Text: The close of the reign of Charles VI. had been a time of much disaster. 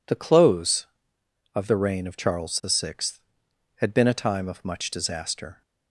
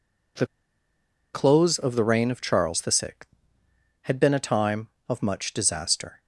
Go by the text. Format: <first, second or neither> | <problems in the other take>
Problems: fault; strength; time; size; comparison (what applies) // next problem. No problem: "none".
first | pauses between "The" and "close"; noticeable; at 0.4 s; 0.87 s long